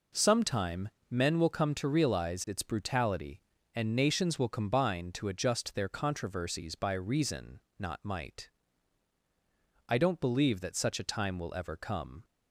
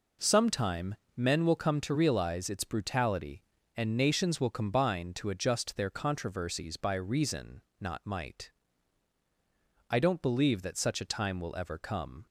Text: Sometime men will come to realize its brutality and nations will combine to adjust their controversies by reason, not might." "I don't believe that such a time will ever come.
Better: neither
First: pauses between "Sometime" and "men"; slight; at 0.8 s; 0.20 s long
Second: pauses between "Sometime" and "men"; slight; at 0.9 s; 0.20 s long

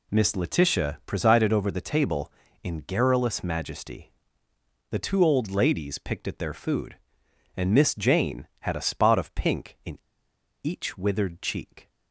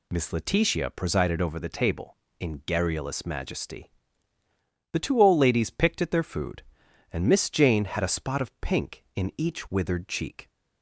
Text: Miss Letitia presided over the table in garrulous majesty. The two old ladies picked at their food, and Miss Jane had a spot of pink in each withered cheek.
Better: second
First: pauses between "in" and "each"; noticeable; at 9.9 s; 0.64 s long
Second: none

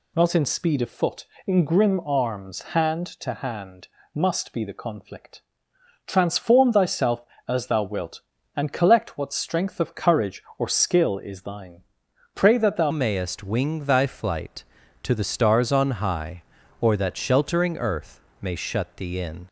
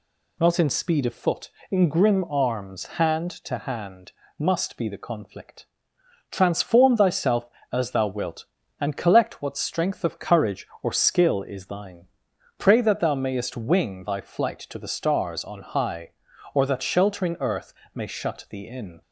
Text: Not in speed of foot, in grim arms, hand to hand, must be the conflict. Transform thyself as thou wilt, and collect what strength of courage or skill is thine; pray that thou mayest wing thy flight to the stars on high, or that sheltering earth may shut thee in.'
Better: second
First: changes voice at "mayest"; from 12.9 s on; 6.5 s long // pauses between "earth" and "may"; slight; at 18.1 s; 0.22 s long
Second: pauses between "earth" and "may"; slight; at 17.7 s; 0.22 s long

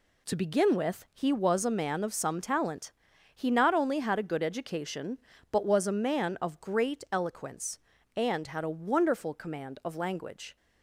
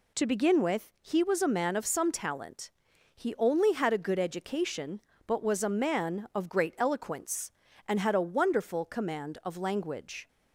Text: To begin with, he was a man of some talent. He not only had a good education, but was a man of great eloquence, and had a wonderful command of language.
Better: first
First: none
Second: skips "not"; at 3.3 s

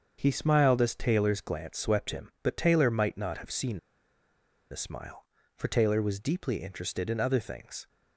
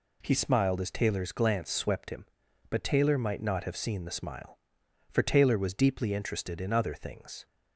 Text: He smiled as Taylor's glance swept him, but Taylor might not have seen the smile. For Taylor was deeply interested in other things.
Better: second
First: starts louder than the rest; until 1.2 s; 7 dB // pauses between "seen" and "the"; noticeable; at 3.7 s; 0.93 s long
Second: none

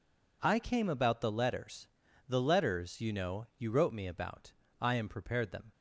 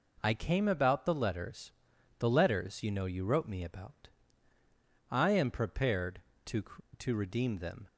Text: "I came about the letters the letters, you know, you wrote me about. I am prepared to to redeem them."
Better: second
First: pauses between "letters" and "the"; at 1.8 s; 0.40 s long // skips "to to redeem"; at 5.5 s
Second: pauses between "letters" and "the"; noticeable; at 1.7 s; 0.48 s long

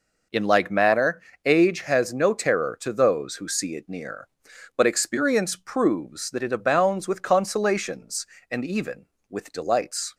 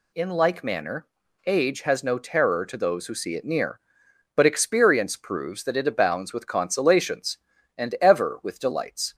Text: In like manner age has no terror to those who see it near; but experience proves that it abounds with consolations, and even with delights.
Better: first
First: pauses between "manner" and "age"; slight; at 1.2 s; 0.24 s long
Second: pauses between "manner" and "age"; at 1.0 s; 0.40 s long // says "ever" for "even"; at 7.9 s

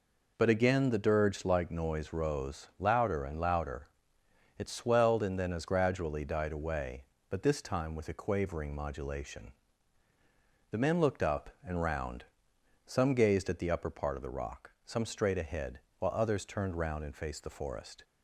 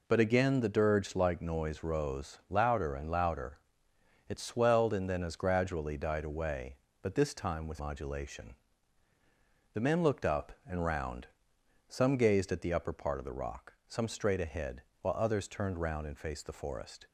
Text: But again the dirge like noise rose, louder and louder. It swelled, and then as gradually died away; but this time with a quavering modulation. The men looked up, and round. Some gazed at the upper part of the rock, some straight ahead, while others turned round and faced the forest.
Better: first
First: none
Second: skips "a quavering"; at 7.7 s

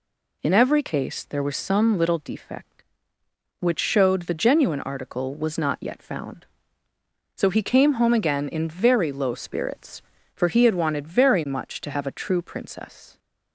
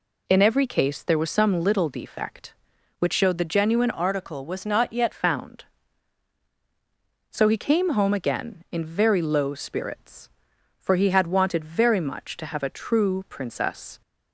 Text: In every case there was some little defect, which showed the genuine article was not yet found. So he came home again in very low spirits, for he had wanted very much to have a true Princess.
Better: first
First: none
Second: changes voice from "article" to "yet"; from 3.9 to 5.1 s; 1.2 s long

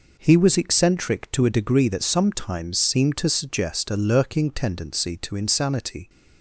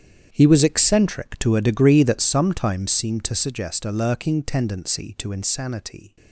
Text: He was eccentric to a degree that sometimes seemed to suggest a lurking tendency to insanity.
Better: first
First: none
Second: gets quieter; strong; throughout; 15 dB

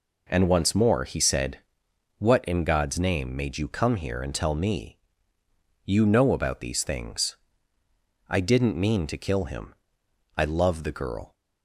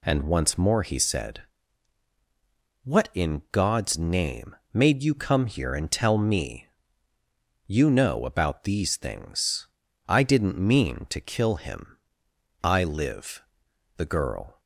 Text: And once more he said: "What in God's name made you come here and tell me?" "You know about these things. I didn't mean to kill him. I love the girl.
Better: first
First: none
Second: pauses between "name" and "made"; slight; at 4.5 s; 0.18 s long // says "live" for "love"; at 12.8 s

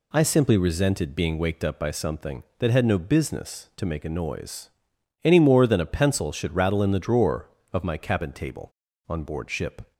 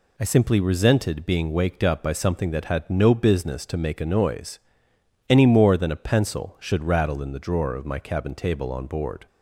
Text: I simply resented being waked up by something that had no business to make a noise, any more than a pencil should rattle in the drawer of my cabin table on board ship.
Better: first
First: none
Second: stops before "ship"; at 9.2 s

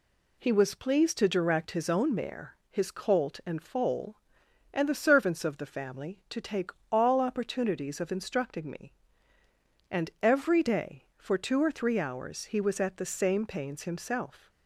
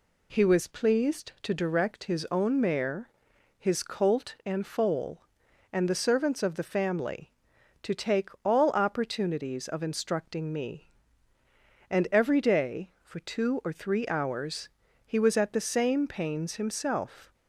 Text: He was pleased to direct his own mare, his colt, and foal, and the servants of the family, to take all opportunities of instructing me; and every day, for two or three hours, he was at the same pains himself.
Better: neither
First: pauses between "take" and "all"; slight; at 6.7 s; 0.20 s long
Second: pauses between "take" and "all"; slight; at 8.2 s; 0.16 s long

